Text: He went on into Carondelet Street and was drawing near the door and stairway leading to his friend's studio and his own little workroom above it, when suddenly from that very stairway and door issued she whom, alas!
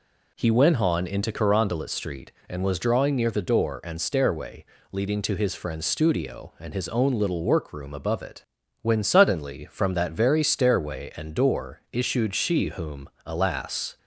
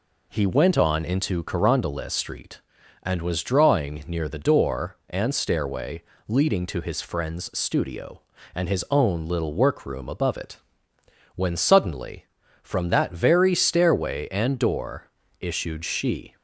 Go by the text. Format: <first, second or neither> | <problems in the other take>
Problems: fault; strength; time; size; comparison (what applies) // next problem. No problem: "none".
first | pauses between "stairway" and "leading"; slight; at 6.0 s; 0.24 s long; slight in the first // pauses between "door" and "issued"; slight; at 15.0 s; 0.32 s long // stops before "whom alas"; at 16.3 s